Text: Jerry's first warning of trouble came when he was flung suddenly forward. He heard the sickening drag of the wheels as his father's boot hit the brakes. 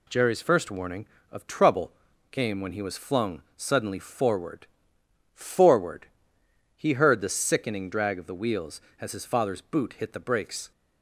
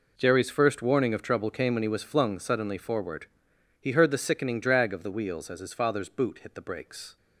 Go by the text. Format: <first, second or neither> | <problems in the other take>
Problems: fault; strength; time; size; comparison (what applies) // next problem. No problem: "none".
second | pauses between "trouble" and "came"; at 1.9 s; 0.40 s long // pauses between "flung" and "suddenly"; slight; at 3.4 s; 0.16 s long // says "forward" twice; at 5.3 s